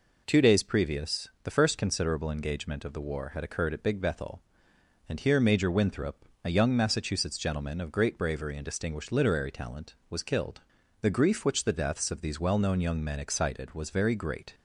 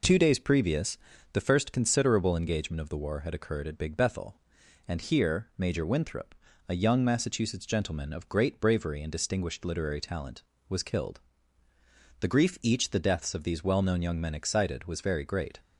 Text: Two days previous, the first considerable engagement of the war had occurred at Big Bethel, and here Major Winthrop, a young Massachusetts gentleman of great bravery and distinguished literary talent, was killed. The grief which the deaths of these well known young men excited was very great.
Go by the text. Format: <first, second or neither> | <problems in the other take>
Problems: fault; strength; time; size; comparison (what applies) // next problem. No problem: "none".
first | says "each" for "which"; at 12.6 s